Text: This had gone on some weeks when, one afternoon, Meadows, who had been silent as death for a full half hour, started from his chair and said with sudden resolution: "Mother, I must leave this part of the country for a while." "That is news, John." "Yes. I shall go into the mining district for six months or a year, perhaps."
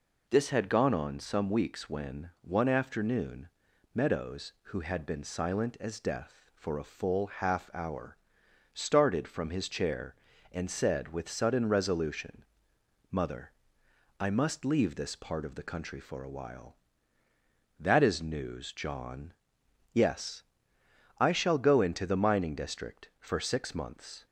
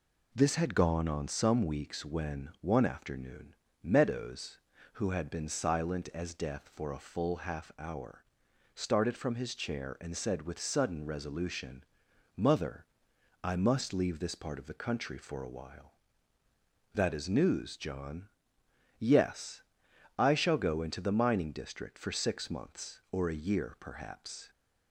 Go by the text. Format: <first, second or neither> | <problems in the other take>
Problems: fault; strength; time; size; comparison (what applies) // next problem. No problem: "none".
second | stops before "or a year perhaps"; at 24.2 s